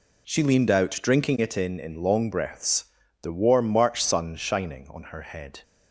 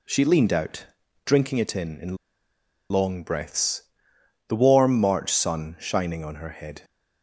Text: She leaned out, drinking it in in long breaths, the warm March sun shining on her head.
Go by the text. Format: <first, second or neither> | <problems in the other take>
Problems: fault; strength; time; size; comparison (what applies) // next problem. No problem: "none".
first | pauses between "in" and "long"; noticeable; at 2.1 s; 0.75 s long